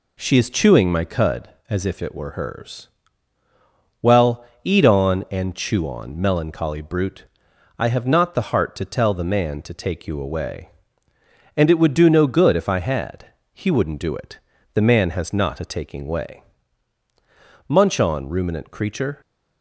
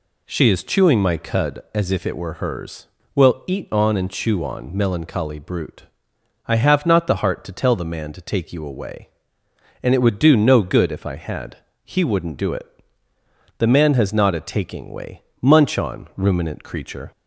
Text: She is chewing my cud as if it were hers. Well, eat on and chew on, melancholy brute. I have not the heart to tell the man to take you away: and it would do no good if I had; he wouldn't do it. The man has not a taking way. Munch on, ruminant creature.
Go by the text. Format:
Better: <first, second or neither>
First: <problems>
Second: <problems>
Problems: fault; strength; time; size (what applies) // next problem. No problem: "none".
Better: neither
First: none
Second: none